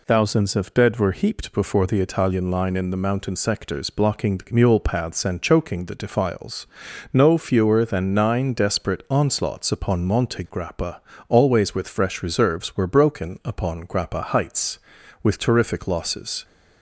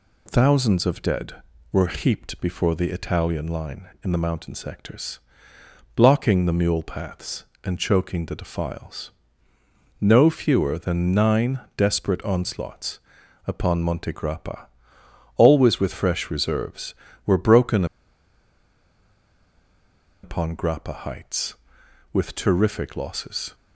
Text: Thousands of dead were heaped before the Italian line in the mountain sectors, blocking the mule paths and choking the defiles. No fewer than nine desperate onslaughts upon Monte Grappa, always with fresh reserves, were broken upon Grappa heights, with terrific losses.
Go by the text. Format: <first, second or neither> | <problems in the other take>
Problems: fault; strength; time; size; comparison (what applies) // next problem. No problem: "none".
first | pauses between "nine" and "desperate"; slight; at 11.6 s; 0.16 s long // pauses between "onslaughts" and "upon"; noticeable; at 12.9 s; 0.48 s long // pauses between "broken" and "upon"; strong; at 17.8 s; 2.3 s long